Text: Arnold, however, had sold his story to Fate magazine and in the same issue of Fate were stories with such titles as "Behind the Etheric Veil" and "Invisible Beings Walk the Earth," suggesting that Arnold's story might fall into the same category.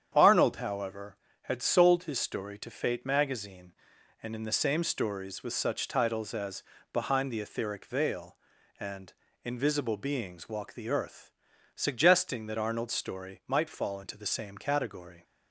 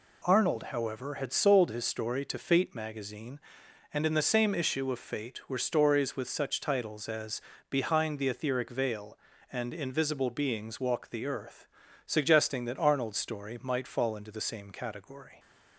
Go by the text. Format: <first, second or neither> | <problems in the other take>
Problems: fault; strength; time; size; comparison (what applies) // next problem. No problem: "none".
second | starts louder than the rest; strong; until 1.1 s; 8.5 dB // skips "issue of Fate were"; at 4.8 s // pauses between "as" and "Behind"; slight; at 6.6 s; 0.32 s long; slight in the second // pauses between "and" and "Invisible"; slight; at 9.1 s; 0.32 s long